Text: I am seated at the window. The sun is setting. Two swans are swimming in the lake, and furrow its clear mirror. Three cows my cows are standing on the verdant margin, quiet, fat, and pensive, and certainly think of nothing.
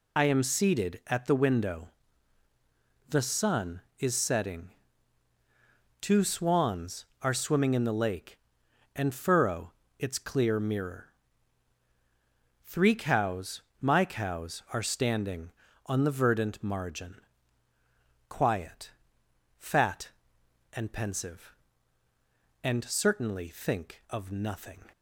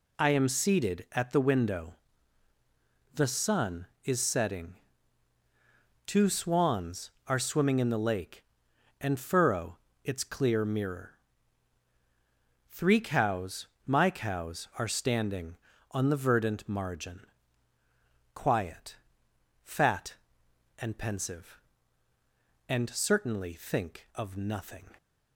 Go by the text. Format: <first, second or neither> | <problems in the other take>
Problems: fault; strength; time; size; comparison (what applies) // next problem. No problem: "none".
second | loses the start of "I"; at 0.1 s; 45 ms // pauses between "furrow" and "its"; slight; at 9.7 s; 0.28 s long; slight in the second // pauses between "cows" and "my"; slight; at 13.6 s; 0.18 s long; slight in the second